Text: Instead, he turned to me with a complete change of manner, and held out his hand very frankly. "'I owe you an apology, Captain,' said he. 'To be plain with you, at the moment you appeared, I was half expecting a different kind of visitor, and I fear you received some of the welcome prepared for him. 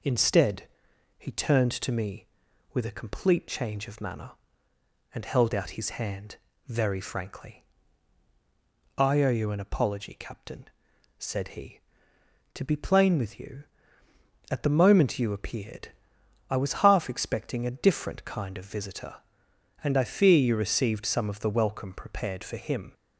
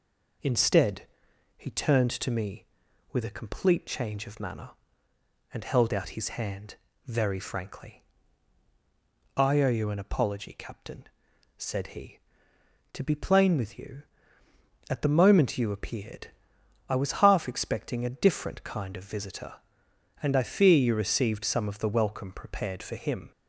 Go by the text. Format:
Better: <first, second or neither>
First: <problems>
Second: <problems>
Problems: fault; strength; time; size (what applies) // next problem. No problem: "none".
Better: neither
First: pauses between "hand" and "very"; slight; at 6.3 s; 0.30 s long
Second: pauses between "hand" and "very"; slight; at 6.7 s; 0.30 s long